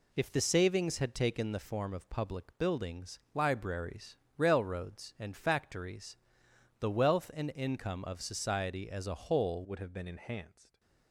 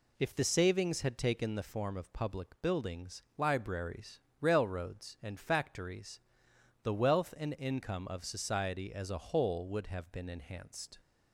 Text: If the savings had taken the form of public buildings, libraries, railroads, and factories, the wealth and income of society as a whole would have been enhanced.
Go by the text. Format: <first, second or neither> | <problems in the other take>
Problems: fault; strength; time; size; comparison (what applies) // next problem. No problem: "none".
second | changes voice at "would"; from 9.6 s on; 1.1 s long